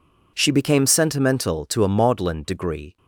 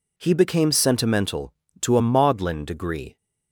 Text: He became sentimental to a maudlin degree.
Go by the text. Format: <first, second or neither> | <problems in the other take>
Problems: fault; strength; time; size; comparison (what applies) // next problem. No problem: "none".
second | says "She" for "He"; at 0.3 s